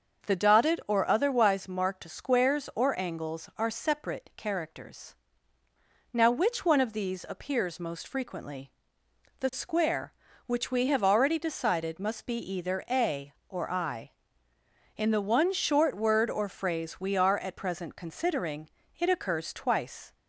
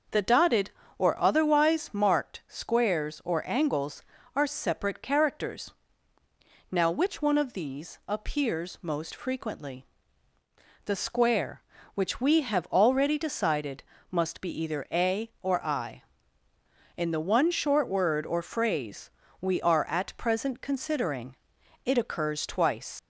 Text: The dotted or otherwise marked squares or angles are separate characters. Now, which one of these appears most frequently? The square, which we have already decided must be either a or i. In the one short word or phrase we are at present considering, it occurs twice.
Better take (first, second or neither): first